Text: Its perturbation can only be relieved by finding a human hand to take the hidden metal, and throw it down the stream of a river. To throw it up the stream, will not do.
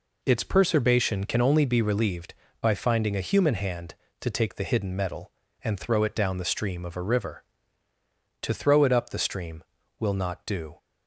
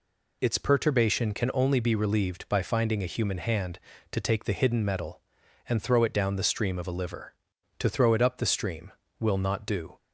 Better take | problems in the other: first | says "liver" for "river"; at 6.9 s

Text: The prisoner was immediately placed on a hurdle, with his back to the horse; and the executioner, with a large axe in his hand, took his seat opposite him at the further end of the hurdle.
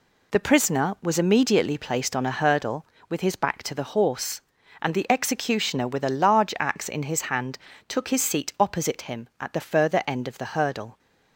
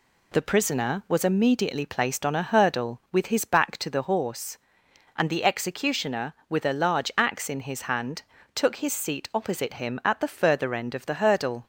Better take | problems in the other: neither | none

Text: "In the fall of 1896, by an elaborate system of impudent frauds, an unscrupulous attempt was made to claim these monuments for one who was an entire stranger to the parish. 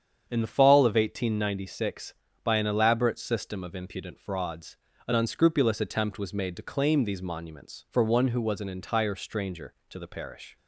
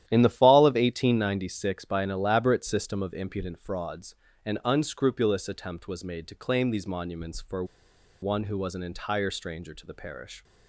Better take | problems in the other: first | starts louder than the rest; strong; until 1.0 s; 12 dB; strong in the first // pauses between "for" and "one"; noticeable; at 7.6 s; 0.57 s long

